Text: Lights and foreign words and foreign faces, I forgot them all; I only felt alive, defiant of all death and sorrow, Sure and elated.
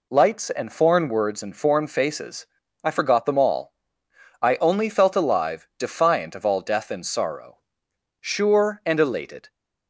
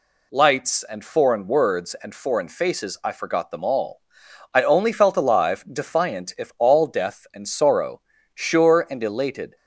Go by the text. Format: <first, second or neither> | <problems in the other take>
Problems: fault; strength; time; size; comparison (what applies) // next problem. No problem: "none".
first | says "if" for "of"; at 6.3 s